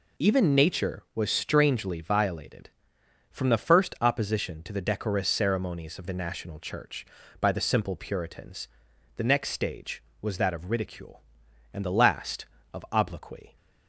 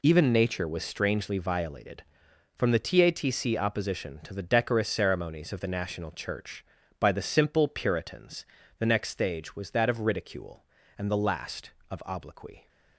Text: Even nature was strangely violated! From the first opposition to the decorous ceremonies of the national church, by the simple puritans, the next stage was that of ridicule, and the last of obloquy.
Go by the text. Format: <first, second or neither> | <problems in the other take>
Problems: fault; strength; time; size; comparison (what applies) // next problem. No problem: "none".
first | says "tatc" for "first"; at 2.7 s